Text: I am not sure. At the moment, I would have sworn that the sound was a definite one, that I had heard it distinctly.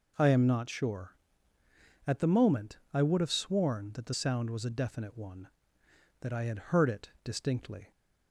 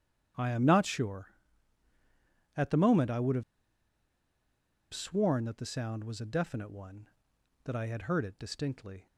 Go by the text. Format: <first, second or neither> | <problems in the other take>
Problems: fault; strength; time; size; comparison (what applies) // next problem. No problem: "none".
first | starts louder than the rest; strong; until 2.6 s; 9 dB // pauses between "have" and "sworn"; strong; at 3.4 s; 1.5 s long